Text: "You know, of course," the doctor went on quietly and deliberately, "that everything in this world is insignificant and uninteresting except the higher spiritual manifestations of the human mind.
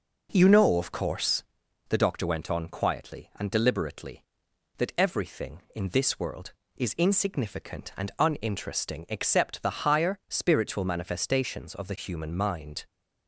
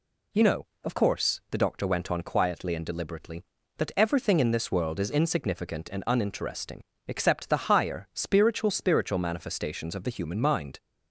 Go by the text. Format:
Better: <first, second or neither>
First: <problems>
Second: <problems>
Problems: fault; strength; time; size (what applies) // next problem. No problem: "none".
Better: first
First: none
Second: pauses between "uninteresting" and "except"; slight; at 6.8 s; 0.26 s long // says "spiritual" twice; at 8.7 s